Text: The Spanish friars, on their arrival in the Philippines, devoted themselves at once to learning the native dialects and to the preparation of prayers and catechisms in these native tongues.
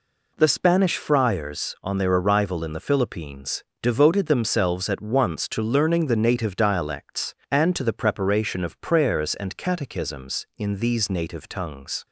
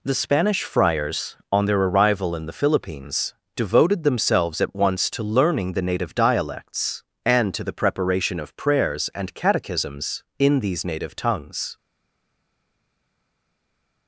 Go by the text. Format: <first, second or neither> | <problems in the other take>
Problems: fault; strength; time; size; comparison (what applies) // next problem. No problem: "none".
first | stays silent after the last word; from 11.7 s on; 2.3 s long